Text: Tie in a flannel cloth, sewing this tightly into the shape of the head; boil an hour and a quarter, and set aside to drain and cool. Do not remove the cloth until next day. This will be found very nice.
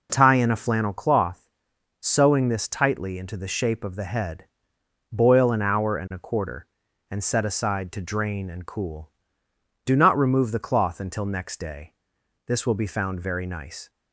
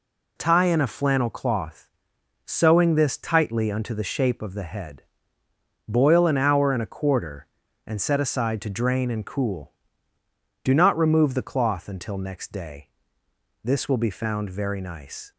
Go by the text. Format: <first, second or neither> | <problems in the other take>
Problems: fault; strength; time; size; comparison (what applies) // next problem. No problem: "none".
first | says "unto" for "into"; at 3.7 s